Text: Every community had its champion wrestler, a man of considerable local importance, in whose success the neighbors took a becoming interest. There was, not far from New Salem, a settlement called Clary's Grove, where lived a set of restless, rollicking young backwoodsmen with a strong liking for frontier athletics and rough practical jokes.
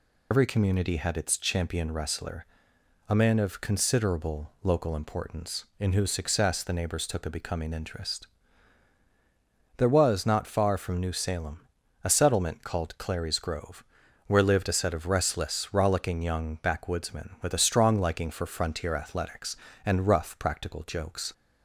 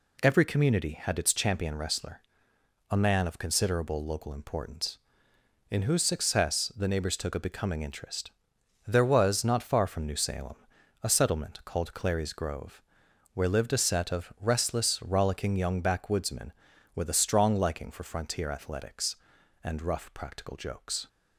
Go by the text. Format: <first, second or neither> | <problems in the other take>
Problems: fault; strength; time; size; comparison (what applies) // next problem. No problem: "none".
second | loses the start of "Every"; at 0.3 s; 90 ms